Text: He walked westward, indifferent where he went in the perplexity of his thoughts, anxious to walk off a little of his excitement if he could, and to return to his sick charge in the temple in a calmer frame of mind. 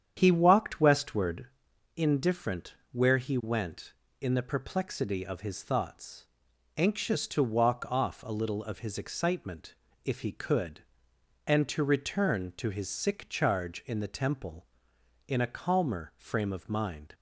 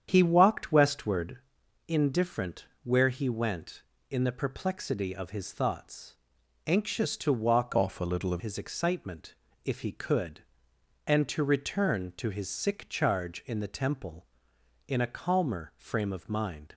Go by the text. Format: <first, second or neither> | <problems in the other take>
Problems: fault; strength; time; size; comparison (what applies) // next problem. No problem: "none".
first | starts louder than the rest; strong; until 1.1 s; 8.5 dB; strong in the first // pauses between "indifferent" and "where"; slight; at 2.6 s; 0.16 s long; slight in the first // changes voice from "off" to "of"; from 7.7 to 8.4 s; 0.7 s long // pauses between "excitement" and "if"; slight; at 9.3 s; 0.28 s long; slight in the first